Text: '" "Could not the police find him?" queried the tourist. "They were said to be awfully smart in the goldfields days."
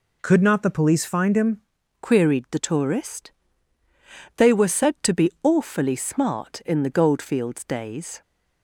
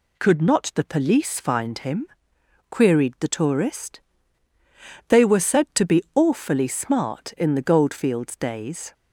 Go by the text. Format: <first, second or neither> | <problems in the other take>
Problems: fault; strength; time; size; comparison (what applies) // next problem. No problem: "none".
second | changes voice from "Could" to "him"; from 0.2 to 1.6 s; 1.4 s long